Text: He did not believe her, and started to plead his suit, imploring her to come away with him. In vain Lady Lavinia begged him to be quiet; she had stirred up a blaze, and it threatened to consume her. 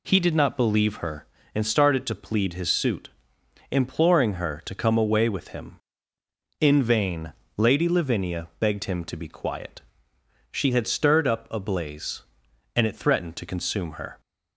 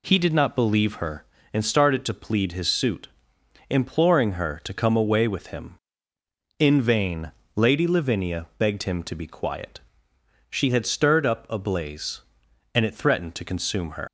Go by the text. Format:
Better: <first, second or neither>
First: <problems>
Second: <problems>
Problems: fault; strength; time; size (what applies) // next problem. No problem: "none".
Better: first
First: pauses between "vain" and "Lady"; slight; at 7.3 s; 0.24 s long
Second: pauses between "vain" and "Lady"; slight; at 7.3 s; 0.24 s long // leaves "her" unfinished; at 14.0 s; 110 ms